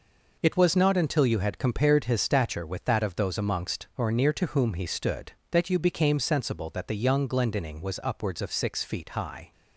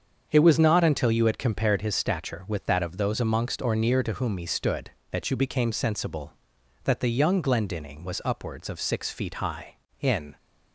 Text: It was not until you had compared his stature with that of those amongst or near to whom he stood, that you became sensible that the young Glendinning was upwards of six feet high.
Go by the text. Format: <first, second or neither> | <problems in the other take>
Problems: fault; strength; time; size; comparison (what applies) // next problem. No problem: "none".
first | starts louder than the rest; until 1.3 s; 7 dB // goes on to say "In"; slight; from 10.0 s on; 0.36 s long